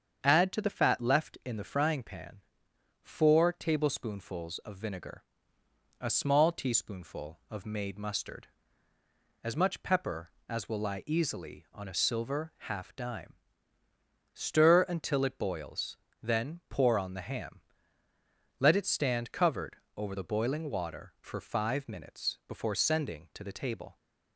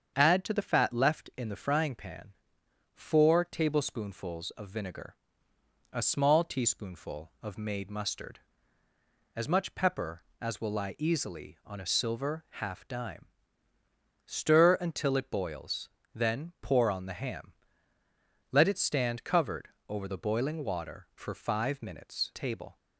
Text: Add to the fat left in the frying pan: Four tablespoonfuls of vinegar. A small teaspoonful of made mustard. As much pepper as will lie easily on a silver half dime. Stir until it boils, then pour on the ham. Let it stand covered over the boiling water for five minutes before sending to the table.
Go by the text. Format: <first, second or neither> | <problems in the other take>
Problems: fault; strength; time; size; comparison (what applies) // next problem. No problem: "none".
first | starts louder than the rest; strong; until 1.1 s; 7.5 dB; strong in the first // pauses between "covered" and "over"; slight; at 19.6 s; 0.20 s long; slight in the first // skips "before sending to the"; at 22.3 s